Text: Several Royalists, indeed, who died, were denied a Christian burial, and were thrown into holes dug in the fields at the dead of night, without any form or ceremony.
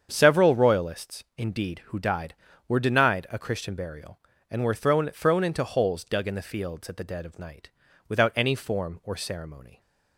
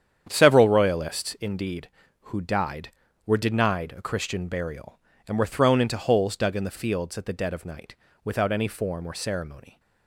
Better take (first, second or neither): second